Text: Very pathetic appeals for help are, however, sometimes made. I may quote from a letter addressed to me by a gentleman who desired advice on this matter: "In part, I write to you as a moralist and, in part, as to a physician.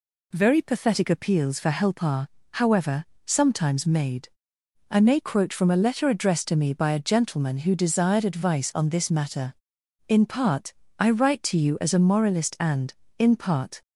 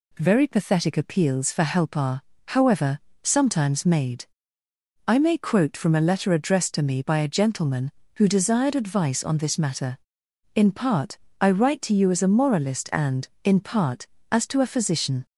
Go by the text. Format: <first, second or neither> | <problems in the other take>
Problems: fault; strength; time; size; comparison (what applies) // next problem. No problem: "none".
second | stops before "as to a physician"; at 13.8 s